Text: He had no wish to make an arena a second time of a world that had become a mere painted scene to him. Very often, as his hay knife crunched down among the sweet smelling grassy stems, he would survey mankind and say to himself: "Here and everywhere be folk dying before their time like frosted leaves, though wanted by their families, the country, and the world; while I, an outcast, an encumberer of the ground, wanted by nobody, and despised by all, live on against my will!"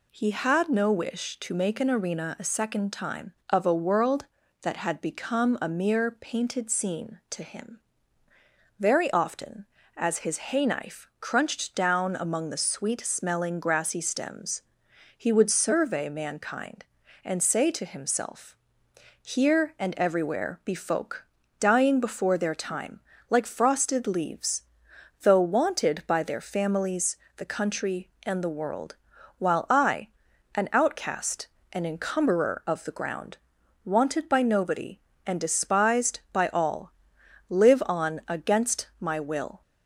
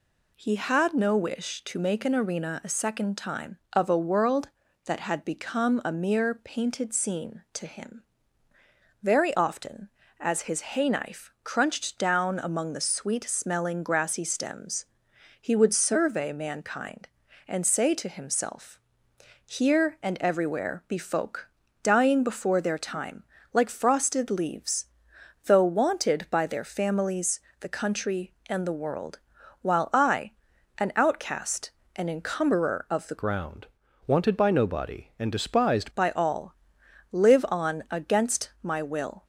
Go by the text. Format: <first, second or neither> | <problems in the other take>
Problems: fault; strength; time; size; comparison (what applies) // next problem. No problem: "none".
first | pauses between "folk" and "dying"; slight; at 21.4 s; 0.34 s long; slight in the first // pauses between "time" and "like"; slight; at 23.2 s; 0.30 s long; slight in the first // changes voice from "ground" to "despised"; from 33.1 to 35.8 s; 2.7 s long